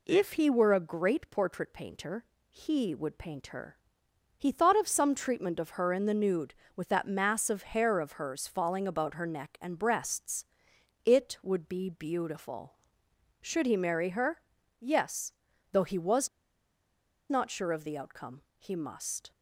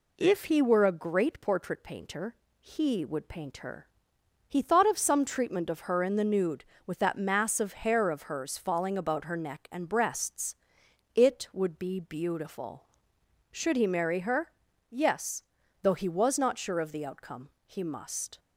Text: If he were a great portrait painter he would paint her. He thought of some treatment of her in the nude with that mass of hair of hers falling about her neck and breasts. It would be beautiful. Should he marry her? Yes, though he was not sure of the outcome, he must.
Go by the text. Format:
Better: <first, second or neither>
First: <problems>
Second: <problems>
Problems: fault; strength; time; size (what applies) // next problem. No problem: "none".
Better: second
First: pauses between "painter" and "he"; slight; at 2.2 s; 0.28 s long // pauses between "was" and "not"; at 16.2 s; 1.0 s long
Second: pauses between "painter" and "he"; slight; at 2.3 s; 0.28 s long